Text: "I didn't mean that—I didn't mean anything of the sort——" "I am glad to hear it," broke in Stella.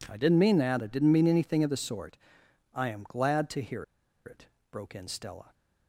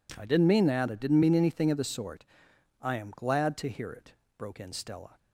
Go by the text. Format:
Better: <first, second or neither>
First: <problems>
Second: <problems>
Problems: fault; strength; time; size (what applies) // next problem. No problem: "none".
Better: second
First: pauses between "hear" and "it"; at 3.8 s; 0.41 s long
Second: none